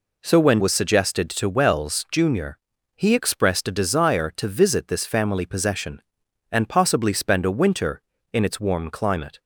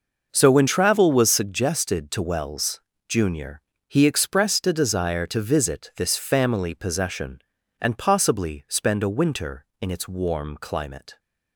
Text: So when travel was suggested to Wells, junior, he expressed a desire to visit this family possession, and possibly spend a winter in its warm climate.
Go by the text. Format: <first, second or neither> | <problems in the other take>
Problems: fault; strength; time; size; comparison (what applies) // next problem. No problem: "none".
second | skips "travel"; at 0.5 s